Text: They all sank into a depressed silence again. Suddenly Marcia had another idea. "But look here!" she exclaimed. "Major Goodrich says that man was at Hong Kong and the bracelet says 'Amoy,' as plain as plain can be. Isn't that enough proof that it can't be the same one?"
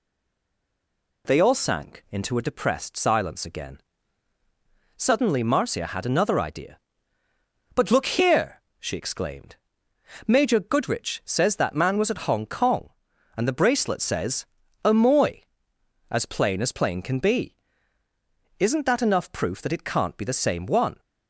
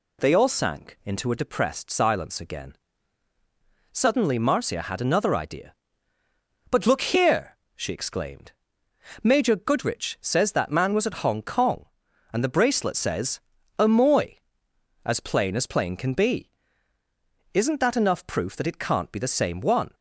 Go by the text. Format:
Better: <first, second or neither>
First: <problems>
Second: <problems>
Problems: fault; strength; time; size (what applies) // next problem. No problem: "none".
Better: second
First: stays silent before the first word; noticeable; until 1.2 s; 1.2 s long // pauses between "says" and "Amoy"; at 14.4 s; 0.38 s long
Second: pauses between "says" and "Amoy"; at 13.4 s; 0.38 s long